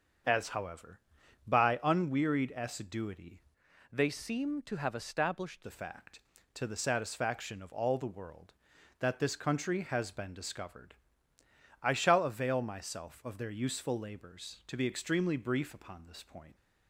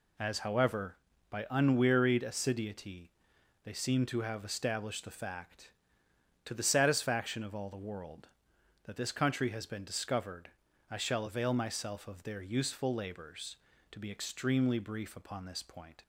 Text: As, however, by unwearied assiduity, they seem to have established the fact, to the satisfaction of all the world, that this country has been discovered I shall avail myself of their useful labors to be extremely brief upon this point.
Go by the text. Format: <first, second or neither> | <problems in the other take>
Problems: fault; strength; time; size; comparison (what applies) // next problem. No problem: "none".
second | starts louder than the rest; until 1.7 s; 7 dB // changes voice from "they" to "established"; from 3.9 to 5.6 s; 1.7 s long // pauses between "discovered" and "I"; noticeable; at 10.9 s; 0.88 s long; also in the second